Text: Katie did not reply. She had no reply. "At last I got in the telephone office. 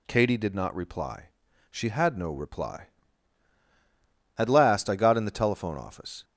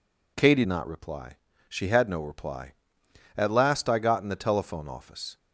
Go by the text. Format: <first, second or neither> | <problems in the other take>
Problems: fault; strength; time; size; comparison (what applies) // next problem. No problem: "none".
first | skips "did"; at 0.6 s